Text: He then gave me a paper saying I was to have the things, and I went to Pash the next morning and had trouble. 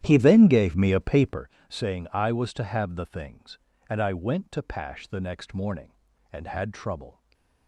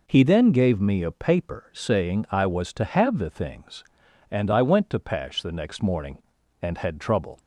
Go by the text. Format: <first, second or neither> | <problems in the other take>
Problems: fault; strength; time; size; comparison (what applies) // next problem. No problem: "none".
second | starts louder than the rest; strong; until 1.5 s; 11.5 dB // pauses between "paper" and "saying"; slight; at 1.4 s; 0.20 s long // stays silent after the last word; slight; from 7.1 s on; 0.5 s long